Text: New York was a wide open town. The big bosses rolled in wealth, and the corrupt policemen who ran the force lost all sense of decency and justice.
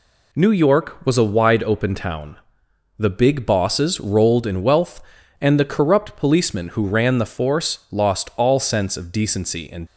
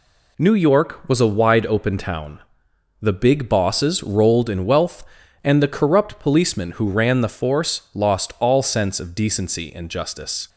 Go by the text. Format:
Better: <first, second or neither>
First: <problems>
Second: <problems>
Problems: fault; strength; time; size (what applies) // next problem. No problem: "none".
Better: second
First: stops before "justice"; at 9.8 s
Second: none